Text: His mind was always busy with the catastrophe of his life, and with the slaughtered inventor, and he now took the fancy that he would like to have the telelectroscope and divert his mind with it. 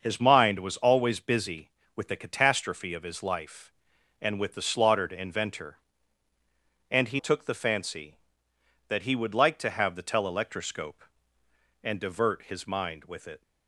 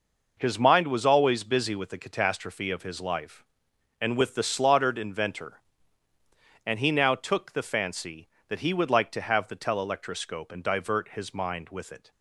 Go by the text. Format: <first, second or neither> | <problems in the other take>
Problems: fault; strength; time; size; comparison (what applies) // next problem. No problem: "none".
second | starts louder than the rest; until 1.0 s; 6 dB // skips "now"; at 7.1 s